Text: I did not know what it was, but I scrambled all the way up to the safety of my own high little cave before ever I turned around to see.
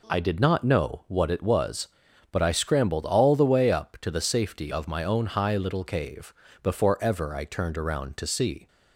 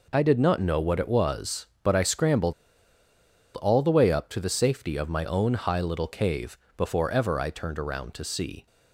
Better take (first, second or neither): first